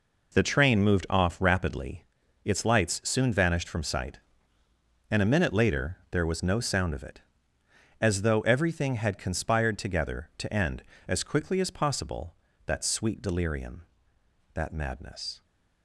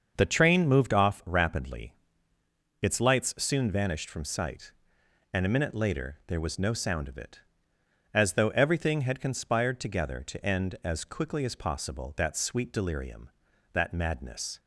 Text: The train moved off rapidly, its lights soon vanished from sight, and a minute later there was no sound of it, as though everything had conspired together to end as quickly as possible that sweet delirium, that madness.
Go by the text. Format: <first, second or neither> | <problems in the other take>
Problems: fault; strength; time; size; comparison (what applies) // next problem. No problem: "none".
first | starts louder than the rest; until 1.3 s; 6.5 dB